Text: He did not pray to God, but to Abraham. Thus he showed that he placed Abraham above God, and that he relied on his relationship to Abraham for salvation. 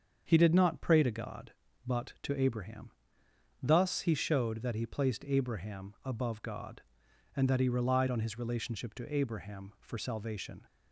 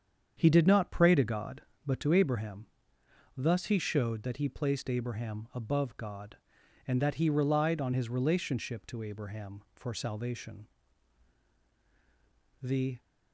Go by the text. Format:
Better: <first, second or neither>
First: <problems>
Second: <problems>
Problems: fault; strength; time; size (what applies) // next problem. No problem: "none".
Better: first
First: starts louder than the rest; strong; until 1.2 s; 7.5 dB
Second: starts louder than the rest; strong; until 1.3 s; 8 dB // goes on to say "The"; slight; from 12.6 s on; 0.38 s long